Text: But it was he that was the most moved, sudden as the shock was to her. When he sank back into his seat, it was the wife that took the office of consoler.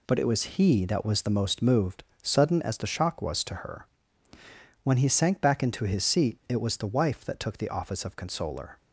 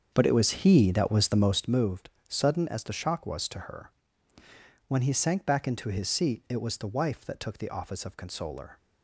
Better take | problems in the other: first | starts louder than the rest; strong; until 1.7 s; 7 dB

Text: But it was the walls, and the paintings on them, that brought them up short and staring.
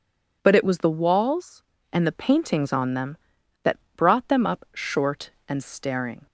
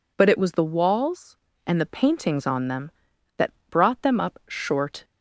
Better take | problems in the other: first | pauses between "that" and "brought"; slight; at 3.5 s; 0.18 s long; slight in the first // stops before "and staring"; at 5.0 s

